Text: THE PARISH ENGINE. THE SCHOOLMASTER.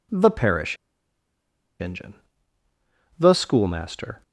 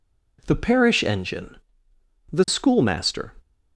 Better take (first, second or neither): second